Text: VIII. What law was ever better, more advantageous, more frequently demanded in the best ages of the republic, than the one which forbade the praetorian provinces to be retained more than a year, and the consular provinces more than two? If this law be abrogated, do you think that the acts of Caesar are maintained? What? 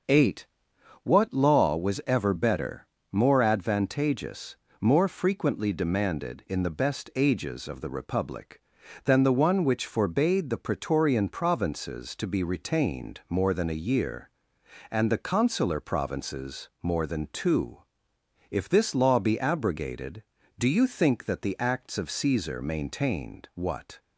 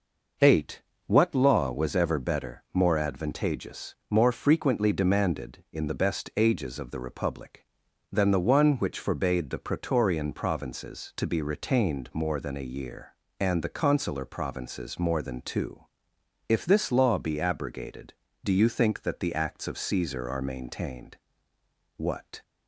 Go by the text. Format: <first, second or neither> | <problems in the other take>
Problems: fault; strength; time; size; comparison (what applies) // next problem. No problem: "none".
second | starts louder than the rest; until 1.6 s; 6.5 dB // skips "are"; at 22.5 s